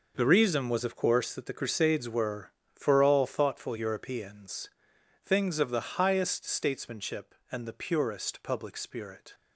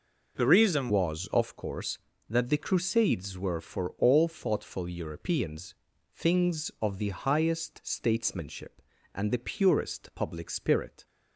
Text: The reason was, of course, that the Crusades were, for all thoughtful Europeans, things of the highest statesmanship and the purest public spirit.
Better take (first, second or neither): first